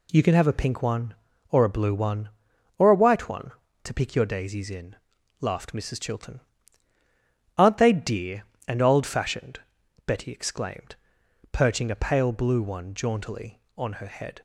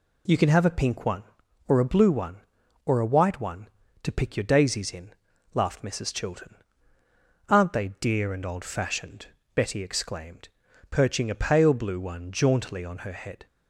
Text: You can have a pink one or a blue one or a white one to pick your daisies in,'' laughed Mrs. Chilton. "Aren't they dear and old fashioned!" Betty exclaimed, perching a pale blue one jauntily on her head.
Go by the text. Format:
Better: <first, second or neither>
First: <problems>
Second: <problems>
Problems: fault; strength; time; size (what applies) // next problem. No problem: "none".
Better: neither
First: none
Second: none